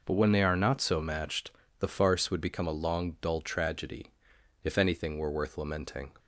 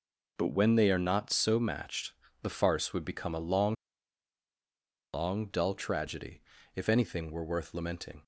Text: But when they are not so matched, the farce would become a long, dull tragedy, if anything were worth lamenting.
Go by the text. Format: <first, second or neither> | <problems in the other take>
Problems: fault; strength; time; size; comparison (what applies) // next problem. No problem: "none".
first | says "long" twice; at 5.1 s